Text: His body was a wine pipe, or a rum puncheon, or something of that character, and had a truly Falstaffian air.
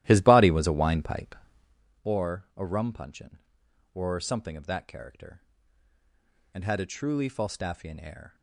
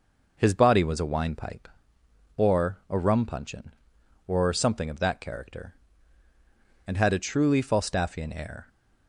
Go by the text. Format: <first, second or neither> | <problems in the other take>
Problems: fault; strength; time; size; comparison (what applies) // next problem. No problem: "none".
second | starts louder than the rest; strong; until 1.9 s; 14 dB